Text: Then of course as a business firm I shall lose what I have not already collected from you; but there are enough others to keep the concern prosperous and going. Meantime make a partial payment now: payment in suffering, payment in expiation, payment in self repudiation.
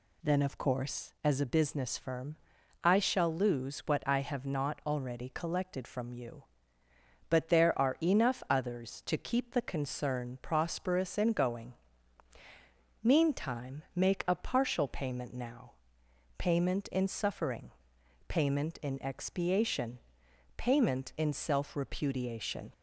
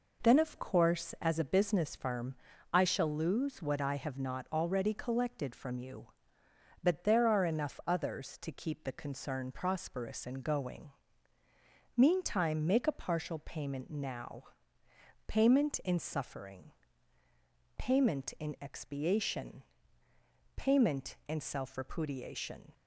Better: neither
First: pauses between "firm" and "I"; noticeable; at 2.3 s; 0.46 s long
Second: pauses between "firm" and "I"; at 2.3 s; 0.38 s long

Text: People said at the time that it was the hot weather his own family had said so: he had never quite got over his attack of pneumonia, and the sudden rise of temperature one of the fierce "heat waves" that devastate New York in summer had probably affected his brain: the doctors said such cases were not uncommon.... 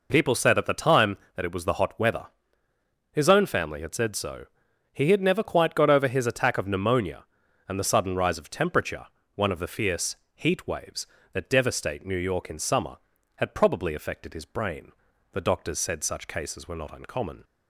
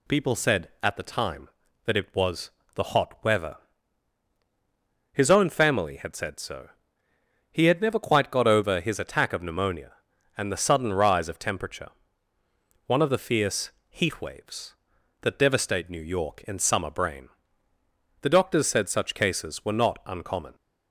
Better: first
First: pauses between "weather" and "his"; noticeable; at 2.2 s; 0.86 s long // pauses between "temperature" and "one"; slight; at 9.0 s; 0.30 s long // pauses between "fierce" and "heat"; slight; at 10.1 s; 0.18 s long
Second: pauses between "was" and "the"; slight; at 2.5 s; 0.24 s long // pauses between "weather" and "his"; strong; at 3.5 s; 1.5 s long // pauses between "temperature" and "one"; noticeable; at 11.8 s; 0.98 s long // pauses between "fierce" and "heat"; slight; at 13.7 s; 0.18 s long // skips "had probably affected his"; at 16.9 s

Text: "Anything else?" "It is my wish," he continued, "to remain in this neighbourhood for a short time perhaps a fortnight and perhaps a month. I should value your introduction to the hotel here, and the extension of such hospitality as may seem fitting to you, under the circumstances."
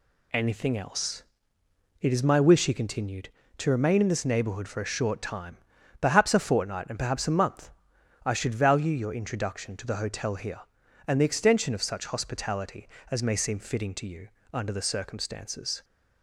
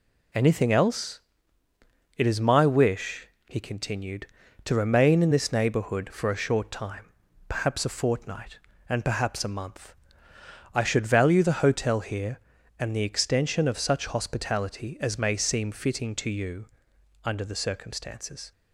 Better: first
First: pauses between "time" and "perhaps"; at 5.5 s; 0.44 s long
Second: pauses between "time" and "perhaps"; slight; at 7.1 s; 0.36 s long // skips "your introduction to"; at 11.4 s

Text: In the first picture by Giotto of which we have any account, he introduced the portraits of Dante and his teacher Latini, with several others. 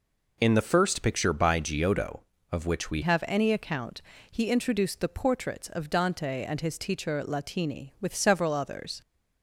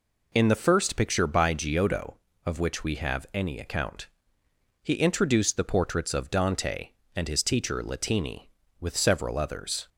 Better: second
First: changes voice at "have"; from 3.0 s on; 6.0 s long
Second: none

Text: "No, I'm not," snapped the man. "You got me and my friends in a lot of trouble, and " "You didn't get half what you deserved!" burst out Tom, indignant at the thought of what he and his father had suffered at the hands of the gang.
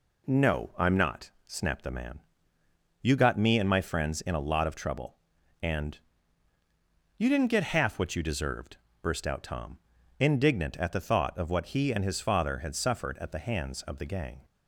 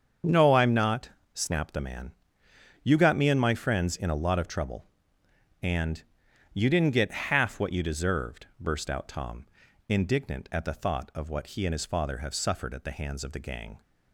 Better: first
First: none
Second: starts louder than the rest; strong; until 1.5 s; 7 dB // says "have" for "had"; at 12.1 s

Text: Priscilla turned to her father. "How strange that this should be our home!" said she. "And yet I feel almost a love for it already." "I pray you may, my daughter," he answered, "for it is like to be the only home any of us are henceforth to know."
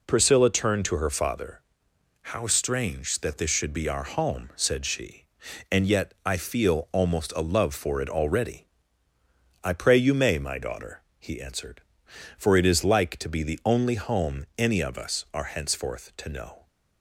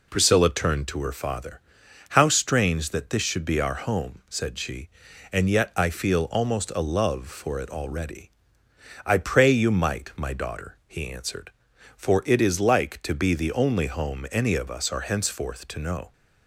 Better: first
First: none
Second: says "might" for "may"; at 9.7 s

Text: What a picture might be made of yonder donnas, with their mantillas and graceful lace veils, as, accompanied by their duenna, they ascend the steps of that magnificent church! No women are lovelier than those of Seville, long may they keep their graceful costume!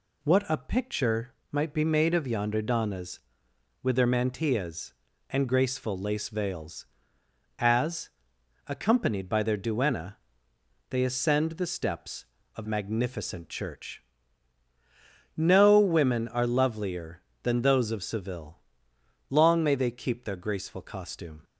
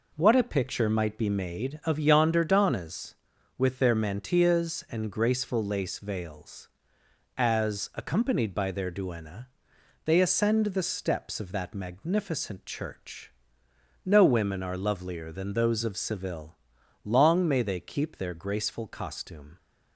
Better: second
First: pauses between "picture" and "might"; slight; at 1.3 s; 0.18 s long // skips "that"; at 12.6 s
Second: none

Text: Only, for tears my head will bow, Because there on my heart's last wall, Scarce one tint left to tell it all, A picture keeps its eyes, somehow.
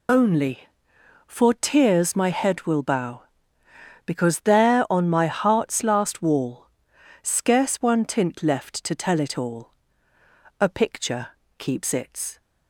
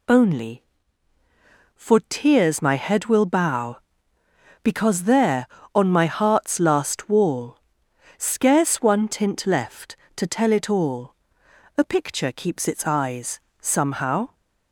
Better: second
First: pauses between "picture" and "keeps"; slight; at 11.2 s; 0.30 s long // stops before "eyes somehow"; at 12.4 s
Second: none

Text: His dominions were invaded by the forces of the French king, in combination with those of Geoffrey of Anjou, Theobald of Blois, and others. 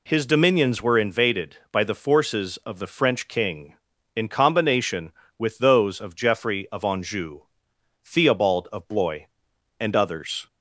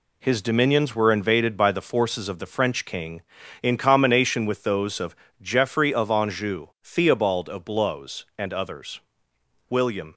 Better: first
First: none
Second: pauses between "of" and "Geoffrey"; slight; at 5.1 s; 0.26 s long // goes on to say "William"; slight; from 9.6 s on; 0.46 s long

